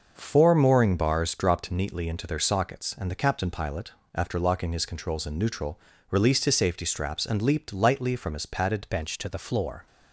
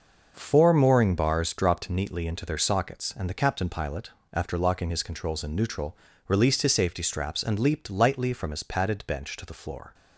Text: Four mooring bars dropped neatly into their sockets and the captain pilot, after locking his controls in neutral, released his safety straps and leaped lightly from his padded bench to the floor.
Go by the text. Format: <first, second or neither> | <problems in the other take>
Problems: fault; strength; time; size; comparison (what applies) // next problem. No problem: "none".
second | changes voice at "bench"; from 8.8 s on; 1.0 s long